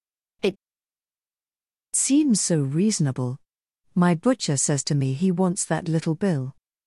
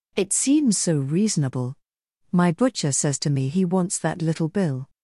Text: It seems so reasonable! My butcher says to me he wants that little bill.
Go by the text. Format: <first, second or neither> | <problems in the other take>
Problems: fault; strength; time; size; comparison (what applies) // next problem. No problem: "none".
second | pauses between "It" and "seems"; strong; at 0.5 s; 1.3 s long